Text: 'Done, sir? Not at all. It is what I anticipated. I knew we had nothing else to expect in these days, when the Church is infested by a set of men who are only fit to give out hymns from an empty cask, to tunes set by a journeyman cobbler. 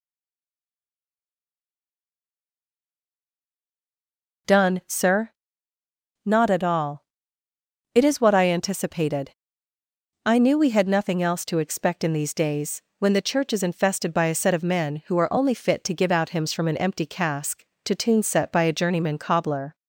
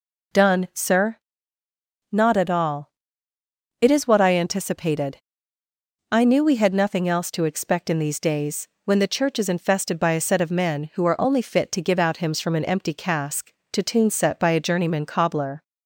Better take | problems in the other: second | stays silent before the first word; strong; until 4.4 s; 4.4 s long

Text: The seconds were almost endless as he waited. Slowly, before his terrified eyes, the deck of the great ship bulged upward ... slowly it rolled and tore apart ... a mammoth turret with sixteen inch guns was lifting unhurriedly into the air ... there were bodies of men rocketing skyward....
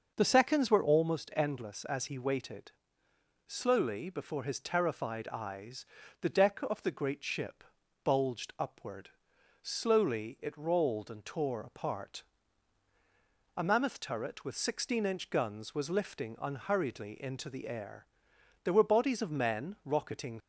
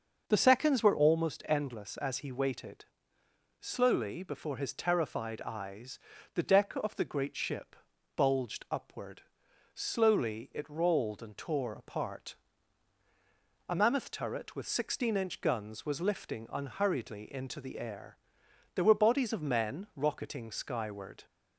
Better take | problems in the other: second | starts louder than the rest; until 1.1 s; 6.5 dB; also in the second // pauses between "ship" and "bulged"; at 7.6 s; 0.40 s long; also in the second // stops before "skyward"; at 20.4 s

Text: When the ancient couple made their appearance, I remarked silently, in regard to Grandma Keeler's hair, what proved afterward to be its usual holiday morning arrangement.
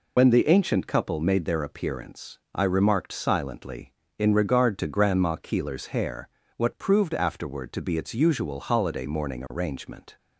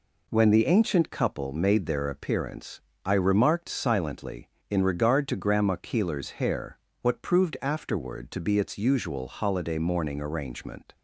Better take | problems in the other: second | loses the start of "When"; at 0.1 s; 65 ms

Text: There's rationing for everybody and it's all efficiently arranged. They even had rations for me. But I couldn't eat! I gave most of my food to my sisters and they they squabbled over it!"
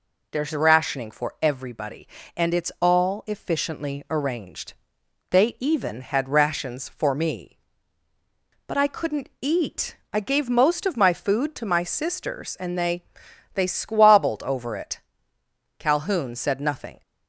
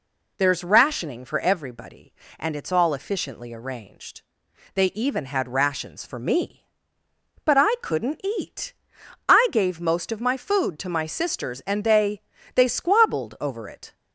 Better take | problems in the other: second | pauses between "they" and "they"; noticeable; at 13.0 s; 0.50 s long; slight in the second // goes on to say "Calhoun said nothing"; noticeable; from 15.7 s on; 1.2 s long

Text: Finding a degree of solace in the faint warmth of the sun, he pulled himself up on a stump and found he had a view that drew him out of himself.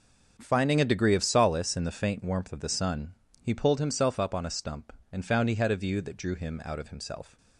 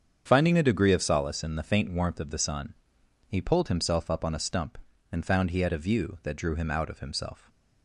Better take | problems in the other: neither | starts louder than the rest; the same in both

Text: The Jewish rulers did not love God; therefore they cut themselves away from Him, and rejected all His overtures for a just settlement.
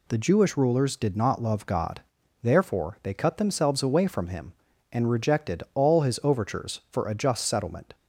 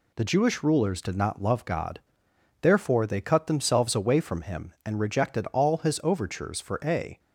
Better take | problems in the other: first | stops before "just settlement"; at 7.1 s

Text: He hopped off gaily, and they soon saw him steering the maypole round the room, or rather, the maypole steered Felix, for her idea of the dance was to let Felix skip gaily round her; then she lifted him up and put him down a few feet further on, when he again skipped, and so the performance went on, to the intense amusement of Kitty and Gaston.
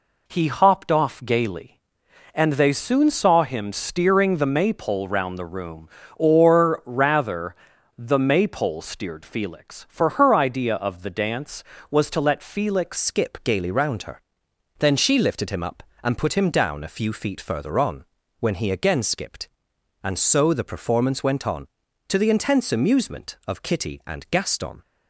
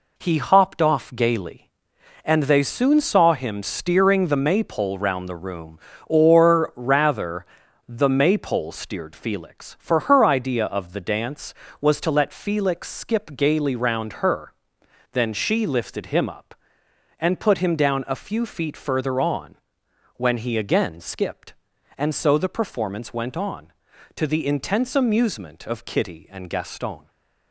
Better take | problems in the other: second | changes voice at "skip"; from 12.9 s on; 11.9 s long

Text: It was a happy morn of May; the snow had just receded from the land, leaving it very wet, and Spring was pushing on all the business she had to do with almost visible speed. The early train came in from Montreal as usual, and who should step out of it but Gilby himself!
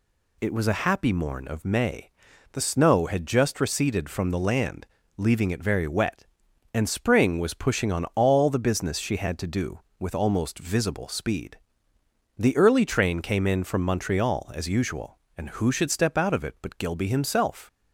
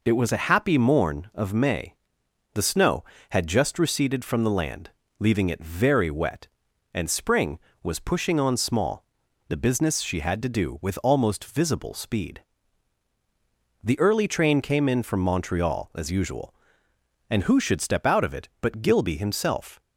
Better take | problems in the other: first | says "small" for "all"; at 8.5 s

